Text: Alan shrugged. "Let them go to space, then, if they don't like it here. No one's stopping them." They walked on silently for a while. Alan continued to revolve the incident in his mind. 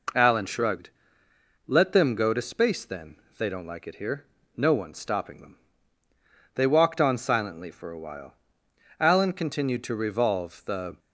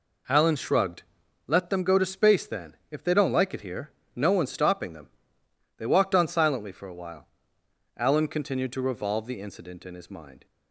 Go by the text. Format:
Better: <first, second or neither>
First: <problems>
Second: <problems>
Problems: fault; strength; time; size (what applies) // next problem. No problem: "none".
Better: second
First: stops before "incident in his mind"; at 10.9 s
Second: none